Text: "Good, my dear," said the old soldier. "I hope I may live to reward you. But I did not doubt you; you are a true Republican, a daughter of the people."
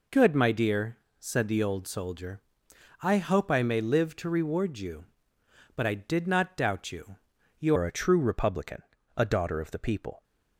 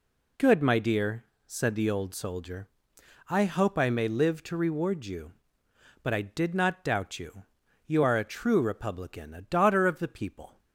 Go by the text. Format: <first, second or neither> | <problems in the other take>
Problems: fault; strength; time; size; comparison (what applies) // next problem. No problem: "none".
second | changes voice at "are"; from 7.7 s on; 2.5 s long